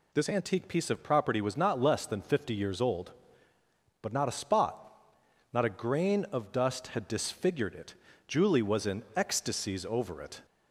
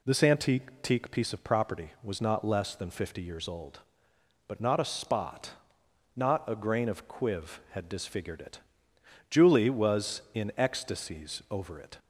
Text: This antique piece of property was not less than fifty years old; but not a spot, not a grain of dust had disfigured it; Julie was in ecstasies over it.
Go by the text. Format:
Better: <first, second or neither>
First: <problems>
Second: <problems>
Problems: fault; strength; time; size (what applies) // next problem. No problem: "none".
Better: first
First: none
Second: says "quiv" for "dust"; at 7.0 s